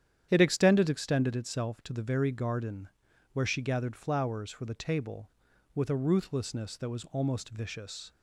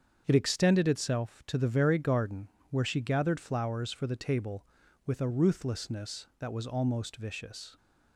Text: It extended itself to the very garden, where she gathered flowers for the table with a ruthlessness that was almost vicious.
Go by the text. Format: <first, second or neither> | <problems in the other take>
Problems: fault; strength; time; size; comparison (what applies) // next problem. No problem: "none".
second | starts louder than the rest; strong; until 1.3 s; 9.5 dB; strong in the second // says "extended" twice; at 0.8 s